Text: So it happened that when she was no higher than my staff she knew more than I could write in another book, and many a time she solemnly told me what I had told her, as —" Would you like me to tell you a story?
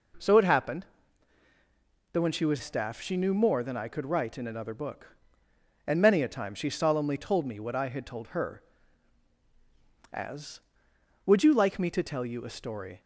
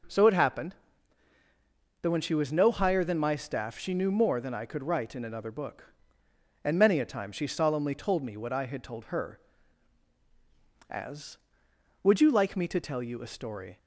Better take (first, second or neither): second